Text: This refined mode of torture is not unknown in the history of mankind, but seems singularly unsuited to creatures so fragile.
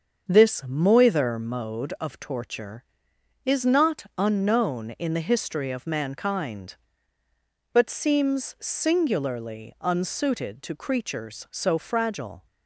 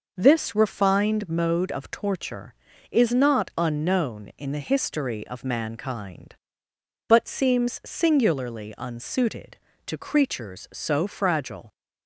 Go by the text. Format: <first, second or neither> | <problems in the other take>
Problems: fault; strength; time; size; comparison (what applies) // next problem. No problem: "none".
second | starts louder than the rest; until 1.3 s; 6.5 dB // says "moither" for "refined"; at 0.6 s // pauses between "not" and "unknown"; slight; at 4.0 s; 0.16 s long